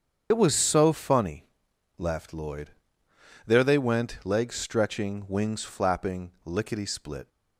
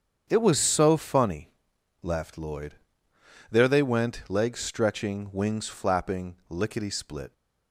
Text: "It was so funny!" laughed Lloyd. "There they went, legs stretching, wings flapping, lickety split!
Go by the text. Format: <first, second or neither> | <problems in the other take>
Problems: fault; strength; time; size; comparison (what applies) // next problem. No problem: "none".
second | loses the start of "It"; at 0.3 s; 60 ms // starts louder than the rest; strong; until 1.3 s; 7.5 dB; strong in the second